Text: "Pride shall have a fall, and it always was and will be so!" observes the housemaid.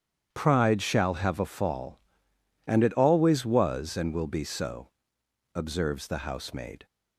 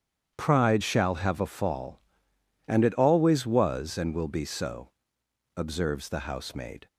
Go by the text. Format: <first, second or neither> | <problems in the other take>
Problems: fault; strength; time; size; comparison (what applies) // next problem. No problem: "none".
neither | starts louder than the rest; strong; the same in both